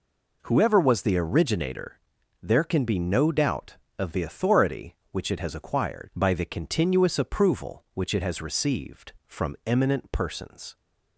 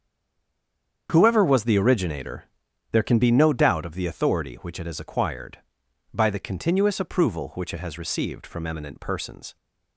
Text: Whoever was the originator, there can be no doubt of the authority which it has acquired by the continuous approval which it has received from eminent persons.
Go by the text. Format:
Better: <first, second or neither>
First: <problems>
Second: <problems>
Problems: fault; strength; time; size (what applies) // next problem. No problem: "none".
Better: first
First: none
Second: stays silent before the first word; until 1.0 s; 1.0 s long // starts louder than the rest; strong; until 2.1 s; 7.5 dB